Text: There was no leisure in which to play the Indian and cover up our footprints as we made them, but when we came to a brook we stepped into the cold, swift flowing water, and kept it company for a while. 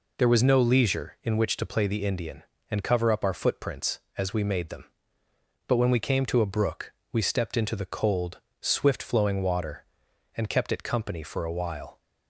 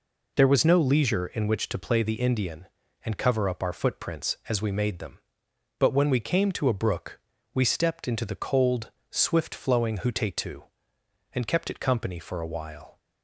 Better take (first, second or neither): first